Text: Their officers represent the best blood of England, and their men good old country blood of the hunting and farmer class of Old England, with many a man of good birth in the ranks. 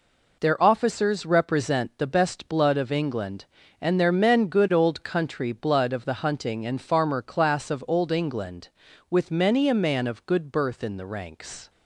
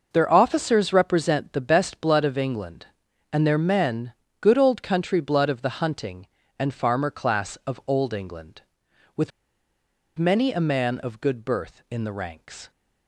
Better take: first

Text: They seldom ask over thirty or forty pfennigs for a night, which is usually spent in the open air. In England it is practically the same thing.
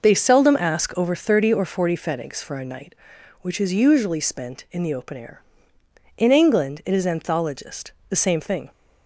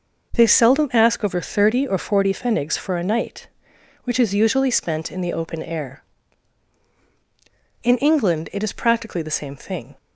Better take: second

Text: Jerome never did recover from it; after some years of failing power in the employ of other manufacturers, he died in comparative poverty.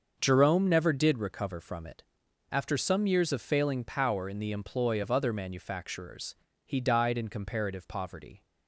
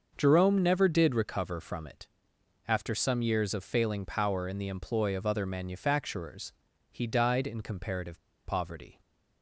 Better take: first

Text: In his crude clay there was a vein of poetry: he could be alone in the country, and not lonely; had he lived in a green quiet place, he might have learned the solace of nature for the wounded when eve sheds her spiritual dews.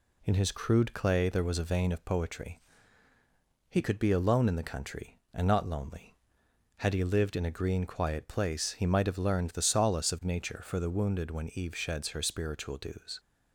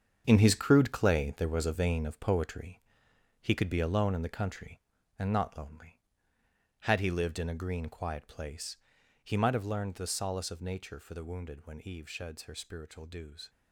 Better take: first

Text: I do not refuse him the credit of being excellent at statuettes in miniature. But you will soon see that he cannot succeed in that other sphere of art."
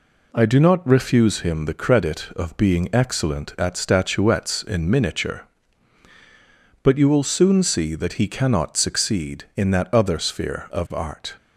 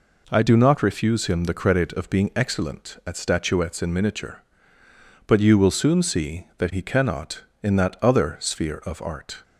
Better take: first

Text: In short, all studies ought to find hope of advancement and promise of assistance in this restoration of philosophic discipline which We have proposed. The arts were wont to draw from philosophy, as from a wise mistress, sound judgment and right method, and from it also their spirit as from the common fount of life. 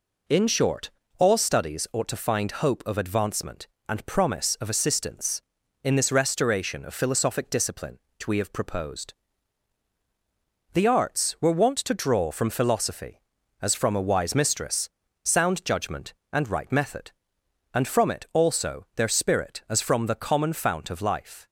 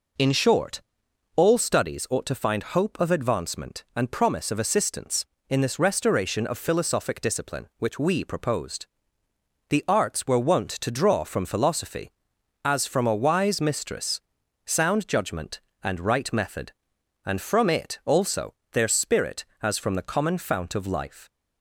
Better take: first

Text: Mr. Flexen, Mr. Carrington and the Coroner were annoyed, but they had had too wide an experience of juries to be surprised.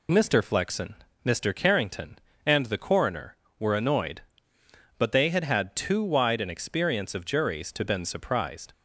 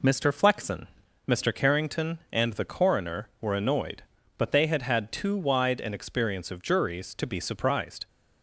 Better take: second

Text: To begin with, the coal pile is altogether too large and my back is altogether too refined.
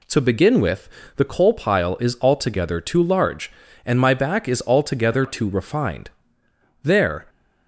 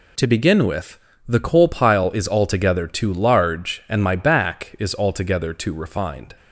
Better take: second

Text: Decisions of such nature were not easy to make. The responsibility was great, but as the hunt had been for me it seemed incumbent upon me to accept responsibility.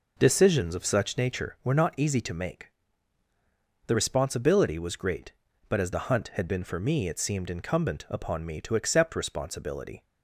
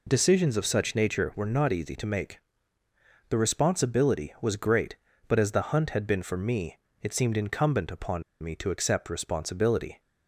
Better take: first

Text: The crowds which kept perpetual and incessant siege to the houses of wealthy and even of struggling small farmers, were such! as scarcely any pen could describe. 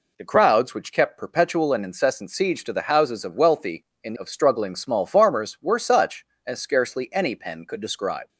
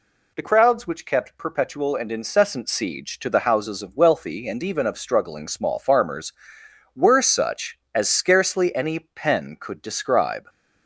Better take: second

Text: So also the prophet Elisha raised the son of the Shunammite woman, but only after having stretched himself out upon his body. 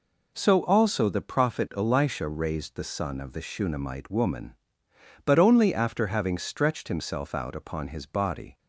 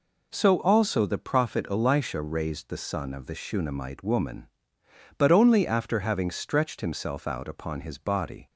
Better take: neither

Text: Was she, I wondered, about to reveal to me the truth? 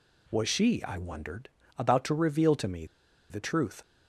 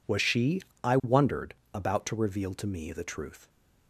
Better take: second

